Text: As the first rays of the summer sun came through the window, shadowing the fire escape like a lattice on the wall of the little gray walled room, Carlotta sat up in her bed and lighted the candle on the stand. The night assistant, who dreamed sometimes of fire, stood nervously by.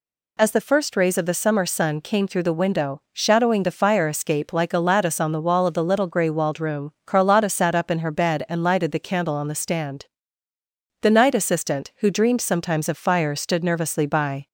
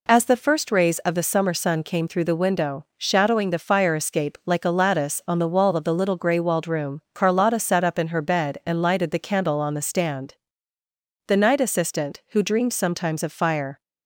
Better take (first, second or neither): first